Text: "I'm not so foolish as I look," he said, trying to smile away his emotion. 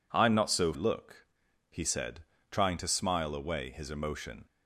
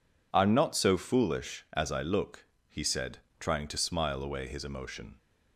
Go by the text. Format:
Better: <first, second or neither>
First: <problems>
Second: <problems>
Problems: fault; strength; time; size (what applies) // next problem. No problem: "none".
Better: second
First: skips "foolish as I"; at 0.7 s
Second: none